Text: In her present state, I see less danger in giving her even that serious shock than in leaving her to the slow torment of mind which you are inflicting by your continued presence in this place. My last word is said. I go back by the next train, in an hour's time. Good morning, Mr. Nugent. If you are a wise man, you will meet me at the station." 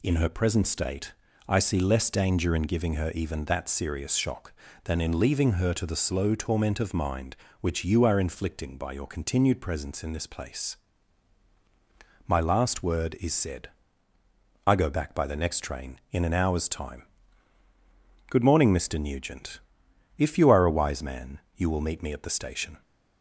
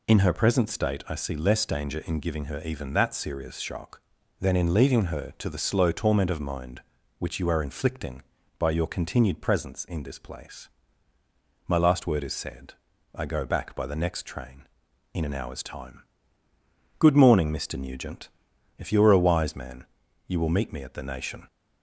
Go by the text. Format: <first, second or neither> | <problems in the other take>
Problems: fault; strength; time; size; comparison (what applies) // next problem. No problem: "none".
first | says "nation" for "station"; at 21.0 s